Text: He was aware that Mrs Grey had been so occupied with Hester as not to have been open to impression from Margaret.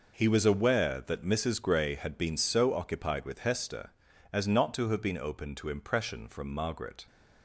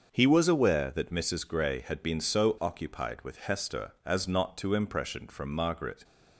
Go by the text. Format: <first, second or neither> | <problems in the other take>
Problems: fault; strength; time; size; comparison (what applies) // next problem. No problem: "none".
first | starts louder than the rest; until 1.1 s; 6.5 dB // skips "have been open to"; at 4.7 s